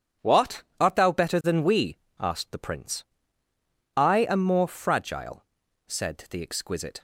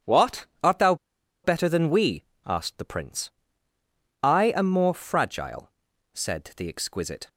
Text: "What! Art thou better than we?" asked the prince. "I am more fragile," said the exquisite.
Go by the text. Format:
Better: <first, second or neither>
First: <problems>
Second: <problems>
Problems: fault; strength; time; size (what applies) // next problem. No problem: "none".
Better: first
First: none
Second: pauses between "thou" and "better"; noticeable; at 0.9 s; 0.48 s long